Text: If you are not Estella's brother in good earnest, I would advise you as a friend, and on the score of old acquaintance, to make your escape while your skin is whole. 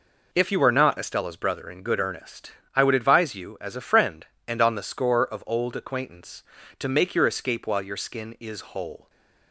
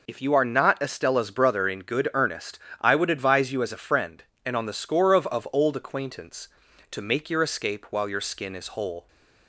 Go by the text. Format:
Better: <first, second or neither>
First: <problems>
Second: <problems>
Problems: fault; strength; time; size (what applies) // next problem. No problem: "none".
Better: first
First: none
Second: says "of" twice; at 5.2 s